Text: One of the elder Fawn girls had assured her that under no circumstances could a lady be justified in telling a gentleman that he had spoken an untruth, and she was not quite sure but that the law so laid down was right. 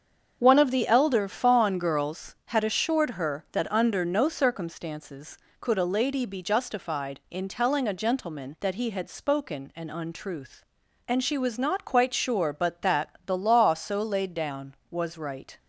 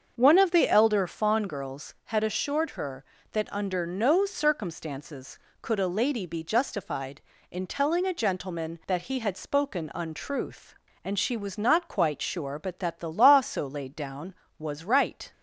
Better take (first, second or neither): first